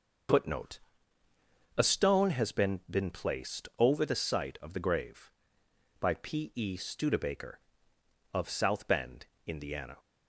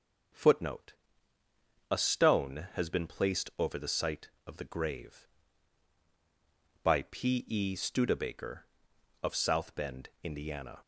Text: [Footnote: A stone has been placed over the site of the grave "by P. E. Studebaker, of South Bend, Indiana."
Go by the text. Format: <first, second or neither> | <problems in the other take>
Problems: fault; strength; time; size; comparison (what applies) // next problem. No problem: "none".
second | starts louder than the rest; until 2.2 s; 6 dB; also in the second // says "been" twice; at 2.8 s